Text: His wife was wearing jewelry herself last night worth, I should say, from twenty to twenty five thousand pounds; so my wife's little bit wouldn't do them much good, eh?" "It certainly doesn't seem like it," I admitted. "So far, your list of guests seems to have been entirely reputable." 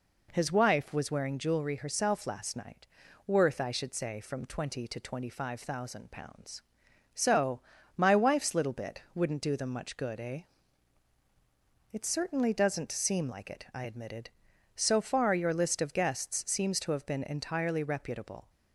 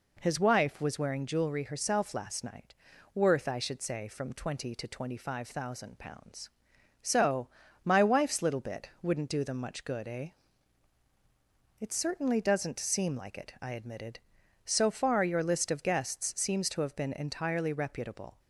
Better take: neither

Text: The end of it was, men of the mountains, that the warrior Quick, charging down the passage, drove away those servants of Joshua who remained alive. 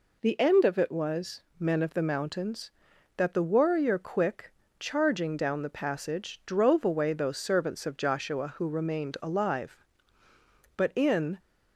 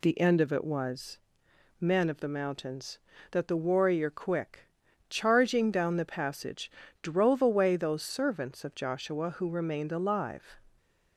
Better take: second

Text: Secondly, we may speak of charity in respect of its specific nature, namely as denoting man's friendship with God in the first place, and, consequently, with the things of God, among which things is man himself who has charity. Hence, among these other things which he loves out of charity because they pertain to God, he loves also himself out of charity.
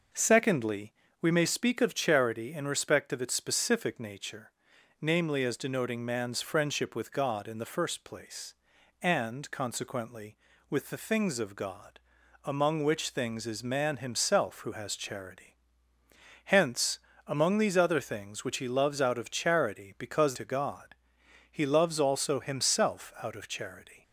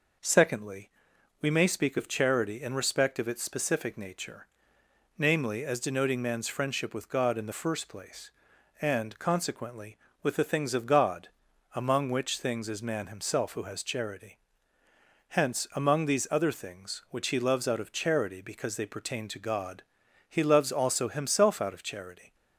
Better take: second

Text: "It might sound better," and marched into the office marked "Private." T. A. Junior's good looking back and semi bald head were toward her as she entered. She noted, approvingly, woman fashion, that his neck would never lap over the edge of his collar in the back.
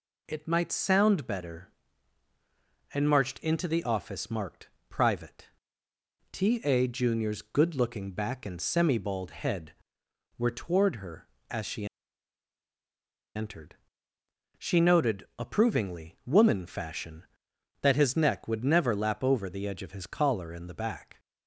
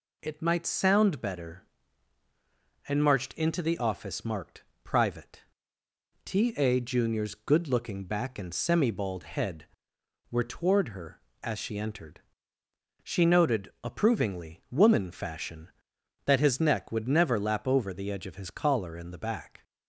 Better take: second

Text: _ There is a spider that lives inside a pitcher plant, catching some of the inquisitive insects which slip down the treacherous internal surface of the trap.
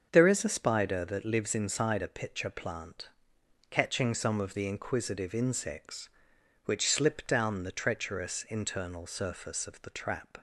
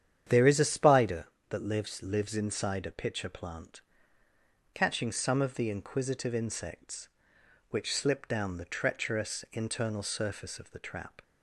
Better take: first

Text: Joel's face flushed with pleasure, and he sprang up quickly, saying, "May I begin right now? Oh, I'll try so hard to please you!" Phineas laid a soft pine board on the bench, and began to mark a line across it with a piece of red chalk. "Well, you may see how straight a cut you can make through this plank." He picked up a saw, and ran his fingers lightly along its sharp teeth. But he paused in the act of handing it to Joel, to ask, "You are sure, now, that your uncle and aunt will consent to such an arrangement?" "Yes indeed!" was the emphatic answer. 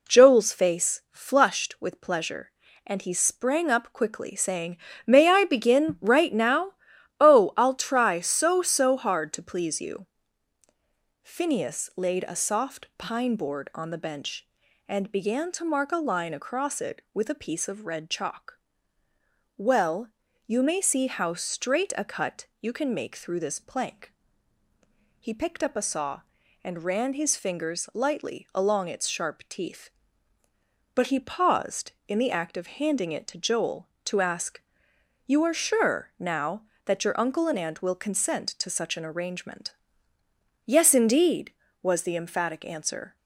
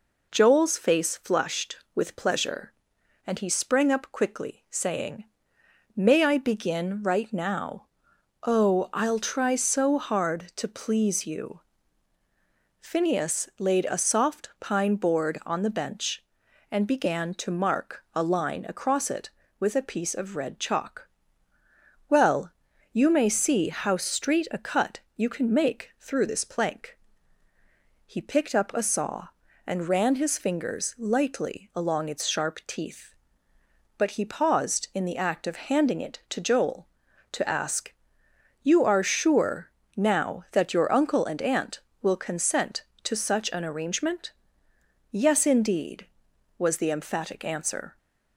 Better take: second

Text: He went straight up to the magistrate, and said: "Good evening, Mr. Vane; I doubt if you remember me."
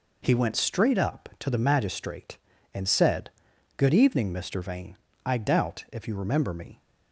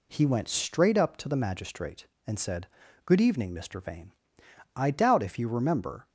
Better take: first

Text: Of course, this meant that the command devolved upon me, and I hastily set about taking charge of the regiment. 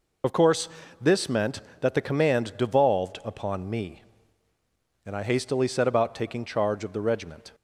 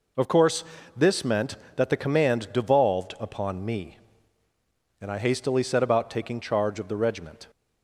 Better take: second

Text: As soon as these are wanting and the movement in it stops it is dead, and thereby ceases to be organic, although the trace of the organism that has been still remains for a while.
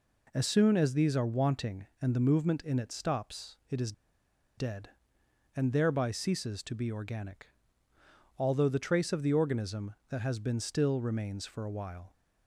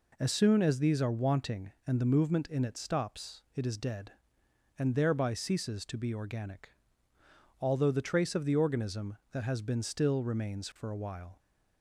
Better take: second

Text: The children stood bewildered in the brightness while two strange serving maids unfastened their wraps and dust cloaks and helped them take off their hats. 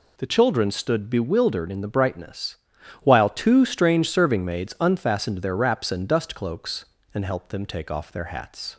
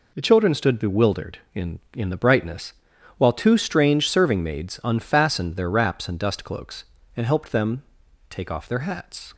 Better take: first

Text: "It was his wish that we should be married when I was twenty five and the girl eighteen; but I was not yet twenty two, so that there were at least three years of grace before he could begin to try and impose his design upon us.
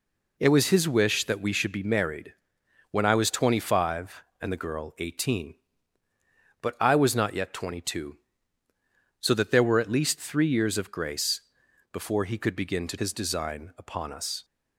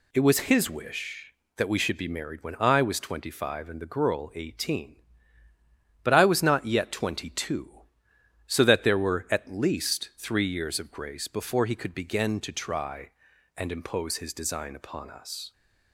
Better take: second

